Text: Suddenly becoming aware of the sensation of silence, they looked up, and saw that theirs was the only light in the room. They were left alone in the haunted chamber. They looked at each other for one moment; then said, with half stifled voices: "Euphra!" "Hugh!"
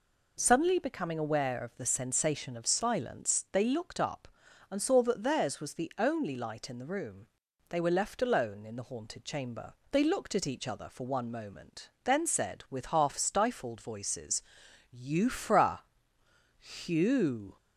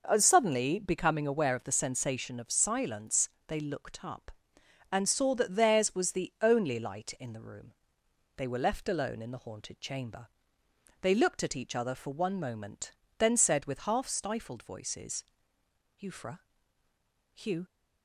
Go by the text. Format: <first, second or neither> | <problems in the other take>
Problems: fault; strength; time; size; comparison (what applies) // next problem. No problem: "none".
neither | none